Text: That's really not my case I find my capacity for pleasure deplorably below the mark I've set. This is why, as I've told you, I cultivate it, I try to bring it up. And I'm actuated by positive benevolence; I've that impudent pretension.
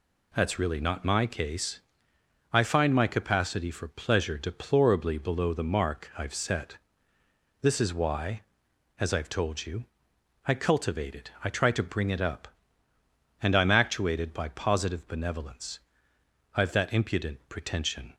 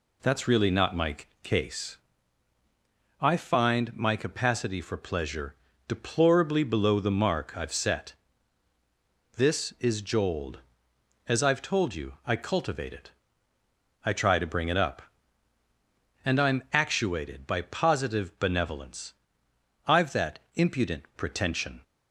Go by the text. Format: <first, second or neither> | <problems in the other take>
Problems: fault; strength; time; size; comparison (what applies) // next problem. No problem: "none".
first | pauses between "my" and "case"; slight; at 1.1 s; 0.26 s long // pauses between "case" and "I"; strong; at 1.9 s; 1.2 s long; noticeable in the first // pauses between "pleasure" and "deplorably"; slight; at 5.5 s; 0.34 s long // says "jold" for "why"; at 9.9 s // pauses between "that" and "impudent"; slight; at 20.3 s; 0.16 s long